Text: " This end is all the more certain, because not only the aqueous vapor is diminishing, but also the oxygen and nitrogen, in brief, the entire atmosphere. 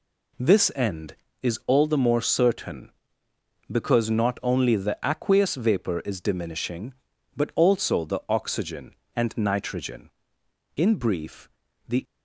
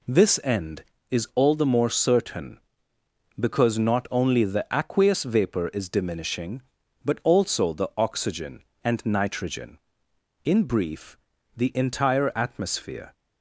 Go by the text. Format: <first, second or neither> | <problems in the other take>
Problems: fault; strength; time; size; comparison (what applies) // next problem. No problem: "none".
second | stops before "entire atmosphere"; at 12.0 s